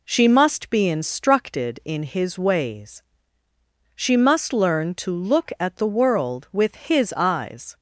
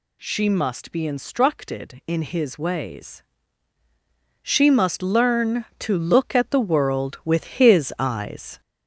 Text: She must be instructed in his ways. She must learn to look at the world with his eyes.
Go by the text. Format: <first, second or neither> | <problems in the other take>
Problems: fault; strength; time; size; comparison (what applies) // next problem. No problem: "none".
first | gets louder; noticeable; throughout; 5 dB